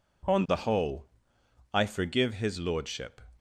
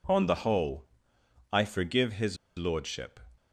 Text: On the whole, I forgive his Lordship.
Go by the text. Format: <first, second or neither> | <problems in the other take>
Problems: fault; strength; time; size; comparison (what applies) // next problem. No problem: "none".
first | pauses between "his" and "Lordship"; slight; at 2.3 s; 0.20 s long